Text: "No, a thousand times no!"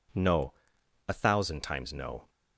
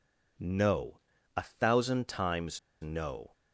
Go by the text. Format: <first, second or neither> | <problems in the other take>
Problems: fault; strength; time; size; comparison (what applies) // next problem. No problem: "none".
first | pauses between "times" and "no"; slight; at 2.5 s; 0.22 s long